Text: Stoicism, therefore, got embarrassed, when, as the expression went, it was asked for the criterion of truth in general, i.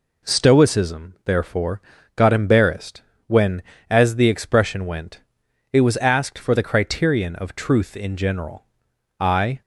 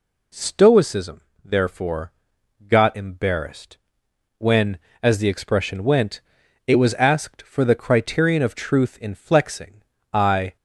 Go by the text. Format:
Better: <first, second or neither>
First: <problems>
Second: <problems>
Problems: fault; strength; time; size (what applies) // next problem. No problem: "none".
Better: first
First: none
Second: says "flexing" for "general"; at 9.1 s